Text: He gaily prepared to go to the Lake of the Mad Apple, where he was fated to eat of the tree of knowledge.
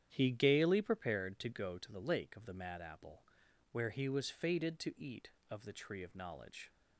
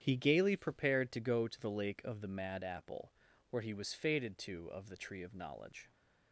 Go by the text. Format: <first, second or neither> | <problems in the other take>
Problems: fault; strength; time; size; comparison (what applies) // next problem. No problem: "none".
first | starts louder than the rest; strong; until 1.0 s; 9 dB; strong in the first // skips "eat"; at 4.6 s